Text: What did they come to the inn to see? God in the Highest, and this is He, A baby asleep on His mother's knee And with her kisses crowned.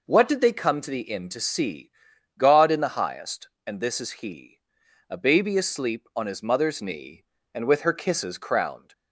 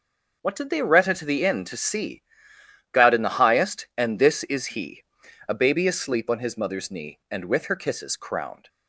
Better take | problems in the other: first | starts louder than the rest; until 1.4 s; 6.5 dB // says "retta" for "come"; at 0.8 s

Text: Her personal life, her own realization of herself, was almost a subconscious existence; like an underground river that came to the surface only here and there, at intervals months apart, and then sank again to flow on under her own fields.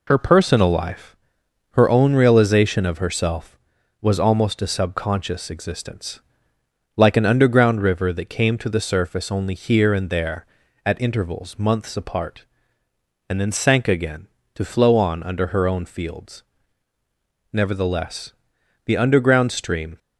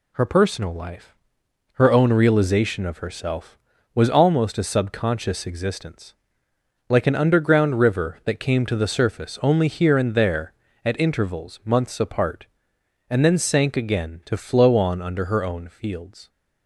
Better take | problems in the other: second | goes on to say "Nevertheless the underground stream"; strong; from 17.5 s on; 2.4 s long

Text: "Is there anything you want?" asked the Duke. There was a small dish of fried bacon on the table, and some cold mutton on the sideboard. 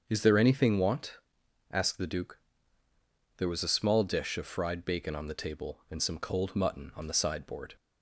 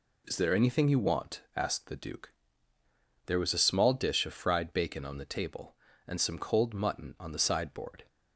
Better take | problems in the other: second | starts louder than the rest; until 1.0 s; 7 dB // skips "you"; at 0.7 s

